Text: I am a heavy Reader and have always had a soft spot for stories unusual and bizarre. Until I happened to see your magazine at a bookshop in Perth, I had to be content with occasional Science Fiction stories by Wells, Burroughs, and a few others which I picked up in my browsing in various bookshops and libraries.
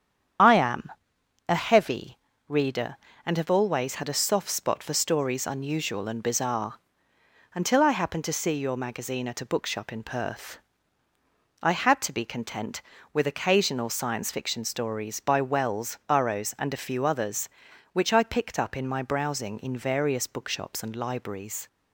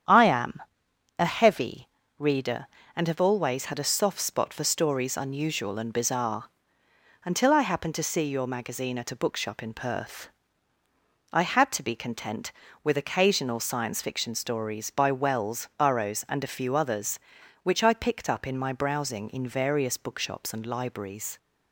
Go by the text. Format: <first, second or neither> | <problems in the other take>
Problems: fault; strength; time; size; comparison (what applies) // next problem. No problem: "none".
second | loses the start of "I"; at 0.3 s; 25 ms // starts louder than the rest; strong; until 1.9 s; 8.5 dB; strong in the second // pauses between "am" and "a"; noticeable; at 0.9 s; 0.56 s long; noticeable in the second // pauses between "heavy" and "Reader"; slight; at 2.1 s; 0.30 s long; slight in the second